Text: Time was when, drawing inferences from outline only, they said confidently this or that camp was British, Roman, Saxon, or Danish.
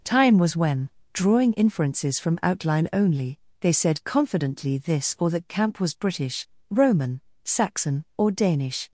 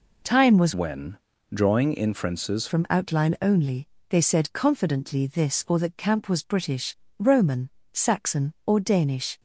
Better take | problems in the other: first | changes voice from "when" to "inferences"; from 0.7 to 2.6 s; 1.9 s long

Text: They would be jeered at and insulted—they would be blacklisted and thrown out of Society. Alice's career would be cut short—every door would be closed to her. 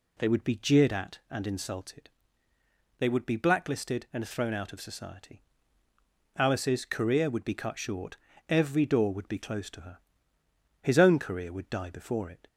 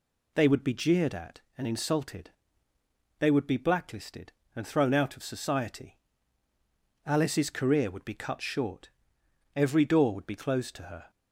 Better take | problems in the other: second | goes on to say "His own career would die before it"; from 10.8 s on; 1.6 s long

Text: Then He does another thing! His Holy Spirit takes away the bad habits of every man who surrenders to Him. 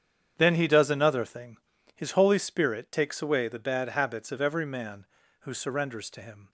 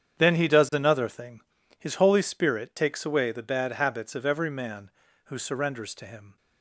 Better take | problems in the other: neither | starts louder than the rest; strong; the same in both

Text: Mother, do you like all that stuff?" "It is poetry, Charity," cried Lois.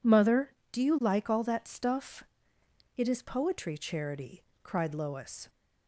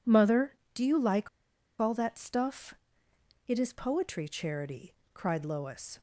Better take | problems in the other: first | pauses between "like" and "all"; noticeable; at 1.2 s; 0.52 s long

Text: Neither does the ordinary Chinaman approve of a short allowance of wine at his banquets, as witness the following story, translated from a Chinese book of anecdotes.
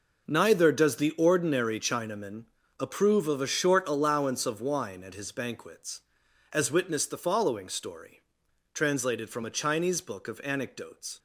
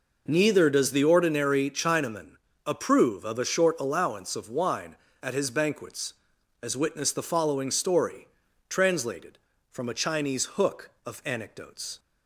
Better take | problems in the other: first | pauses between "Chinaman" and "approve"; slight; at 2.3 s; 0.34 s long; slight in the first // says "hook" for "book"; at 10.5 s

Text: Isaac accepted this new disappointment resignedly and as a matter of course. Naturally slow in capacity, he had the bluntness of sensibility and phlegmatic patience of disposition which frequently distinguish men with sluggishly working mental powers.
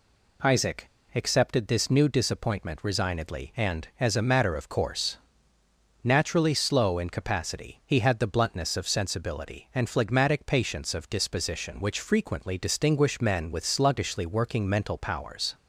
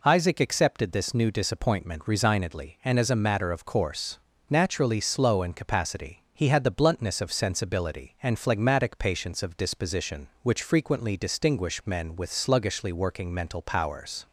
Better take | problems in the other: second | pauses between "Isaac" and "accepted"; slight; at 0.8 s; 0.28 s long

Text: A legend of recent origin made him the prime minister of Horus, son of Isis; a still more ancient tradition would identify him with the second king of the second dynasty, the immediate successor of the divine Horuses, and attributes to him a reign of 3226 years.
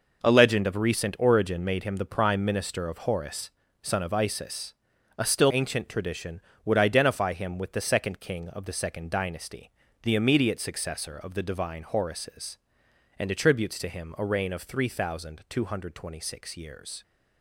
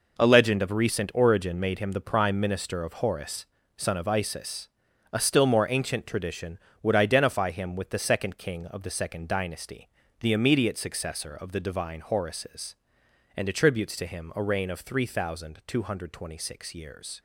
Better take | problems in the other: second | skips "more"; at 5.5 s

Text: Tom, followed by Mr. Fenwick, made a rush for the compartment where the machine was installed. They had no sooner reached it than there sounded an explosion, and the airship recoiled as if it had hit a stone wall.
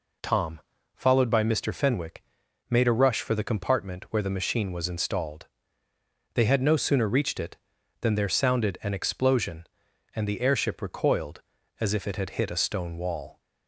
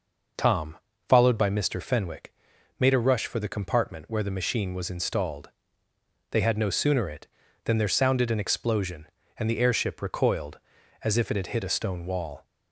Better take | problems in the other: first | skips "reached"; at 7.0 s

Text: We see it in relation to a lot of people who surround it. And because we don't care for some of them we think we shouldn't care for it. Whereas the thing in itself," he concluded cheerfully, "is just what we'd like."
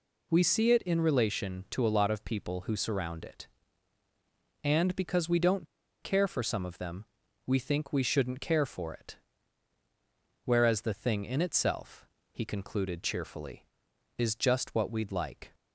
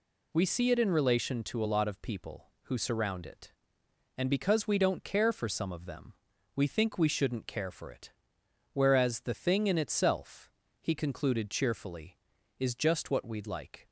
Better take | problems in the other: second | pauses between "don't" and "care"; slight; at 5.6 s; 0.35 s long // pauses between "them" and "we"; at 7.0 s; 0.42 s long; also in the second

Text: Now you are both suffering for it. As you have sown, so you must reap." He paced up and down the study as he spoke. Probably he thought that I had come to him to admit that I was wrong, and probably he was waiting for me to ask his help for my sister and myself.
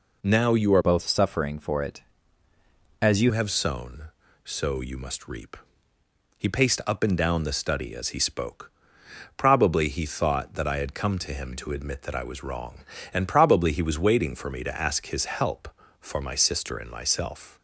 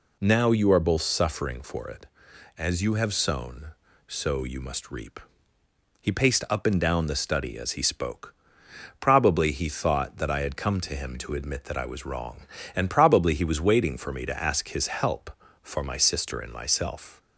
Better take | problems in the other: second | changes voice from "both" to "you"; from 0.8 to 3.3 s; 2.5 s long

